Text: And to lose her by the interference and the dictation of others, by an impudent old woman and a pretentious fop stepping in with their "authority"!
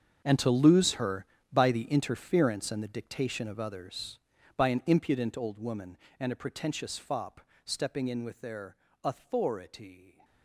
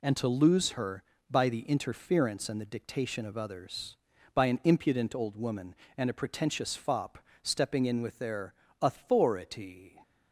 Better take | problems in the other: second | gets quieter; strong; throughout; 16 dB // pauses between "fop" and "stepping"; slight; at 7.4 s; 0.24 s long; slight in the second // pauses between "their" and "authority"; slight; at 8.7 s; 0.26 s long; slight in the second

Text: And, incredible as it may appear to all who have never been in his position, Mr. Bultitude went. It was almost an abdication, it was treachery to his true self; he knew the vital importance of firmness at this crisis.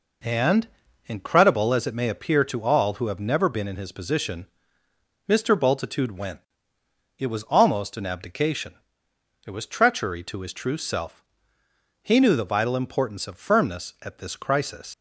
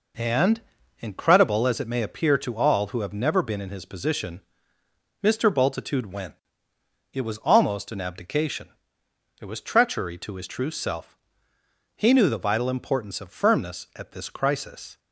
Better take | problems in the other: second | leaves "crisis" unfinished; at 14.9 s; 110 ms

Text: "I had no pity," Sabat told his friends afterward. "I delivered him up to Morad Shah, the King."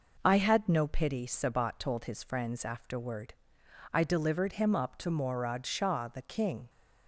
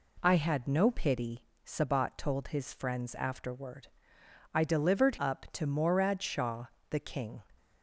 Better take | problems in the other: first | skips "him"; at 5.1 s

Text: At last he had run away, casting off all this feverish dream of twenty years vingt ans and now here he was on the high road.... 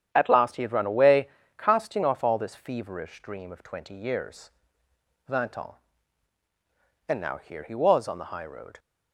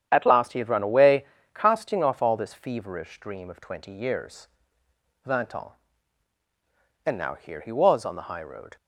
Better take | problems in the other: neither | starts louder than the rest; strong; the same in both // pauses between "years" and "vingt"; noticeable; the same in both

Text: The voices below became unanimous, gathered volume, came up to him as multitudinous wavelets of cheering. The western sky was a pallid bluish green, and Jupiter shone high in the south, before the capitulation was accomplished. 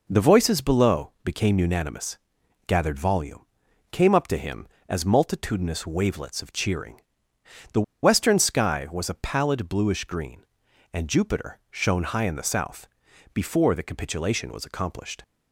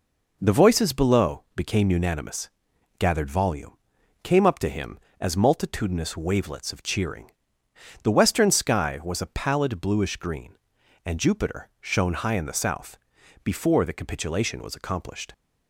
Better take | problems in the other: second | pauses between "The" and "western"; slight; at 7.8 s; 0.20 s long

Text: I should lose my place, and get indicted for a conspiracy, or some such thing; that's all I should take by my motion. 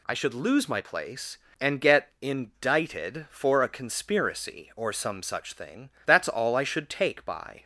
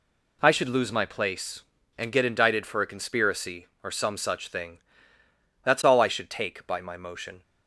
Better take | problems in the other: second | stops before "my motion"; at 7.6 s

